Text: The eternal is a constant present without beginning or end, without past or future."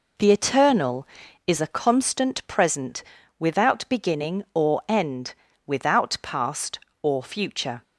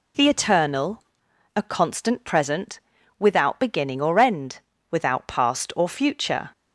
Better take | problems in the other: first | skips "is"; at 1.3 s // pauses between "present" and "without"; at 2.7 s; 0.40 s long; slight in the first

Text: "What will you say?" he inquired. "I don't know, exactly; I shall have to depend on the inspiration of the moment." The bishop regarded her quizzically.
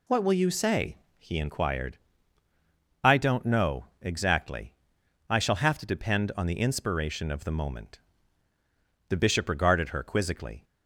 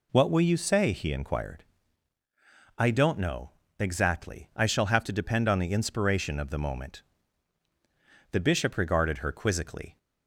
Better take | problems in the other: neither | none

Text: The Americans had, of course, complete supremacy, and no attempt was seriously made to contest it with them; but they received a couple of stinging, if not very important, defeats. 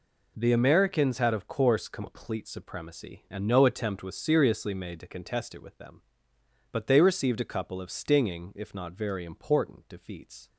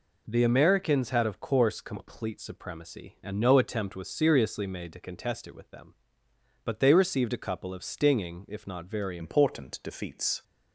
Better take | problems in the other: first | changes voice at "important"; from 9.1 s on; 1.3 s long

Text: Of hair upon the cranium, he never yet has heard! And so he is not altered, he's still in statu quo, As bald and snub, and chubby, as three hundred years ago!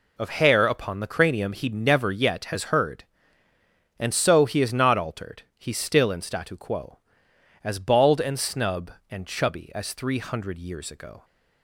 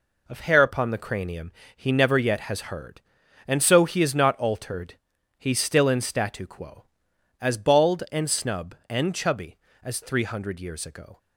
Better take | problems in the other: neither | none

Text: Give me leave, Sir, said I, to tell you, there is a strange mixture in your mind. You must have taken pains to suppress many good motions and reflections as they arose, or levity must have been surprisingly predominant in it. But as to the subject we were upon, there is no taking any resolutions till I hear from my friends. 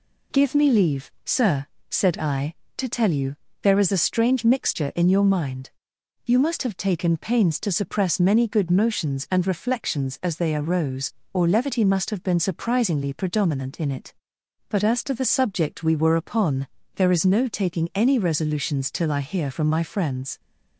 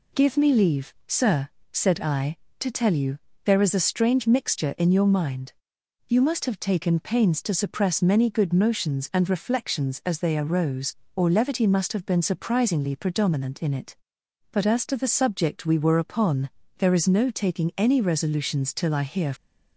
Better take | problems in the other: first | stops before "from my friends"; at 19.3 s

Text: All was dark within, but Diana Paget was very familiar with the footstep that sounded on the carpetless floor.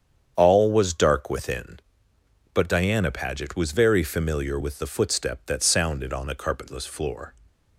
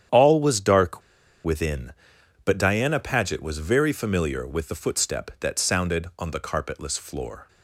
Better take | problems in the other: first | starts louder than the rest; strong; until 1.5 s; 9 dB; strong in the first // pauses between "dark" and "within"; at 1.0 s; 0.43 s long

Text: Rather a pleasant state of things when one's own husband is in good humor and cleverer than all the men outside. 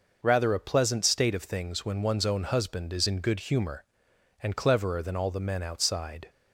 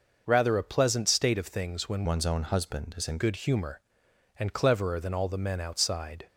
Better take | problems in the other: first | changes voice from "one's" to "in"; from 2.0 to 3.1 s; 1.1 s long

